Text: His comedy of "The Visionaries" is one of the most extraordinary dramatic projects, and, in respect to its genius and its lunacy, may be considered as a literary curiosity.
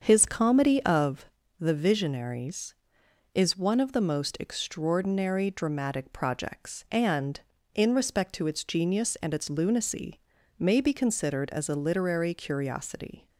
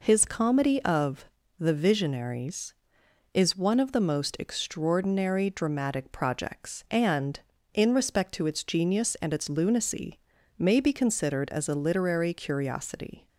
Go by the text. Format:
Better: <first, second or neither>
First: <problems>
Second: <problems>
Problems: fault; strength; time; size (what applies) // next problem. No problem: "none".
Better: second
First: starts louder than the rest; strong; until 1.2 s; 7 dB // pauses between "of" and "The"; slight; at 1.2 s; 0.34 s long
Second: pauses between "of" and "The"; slight; at 1.2 s; 0.34 s long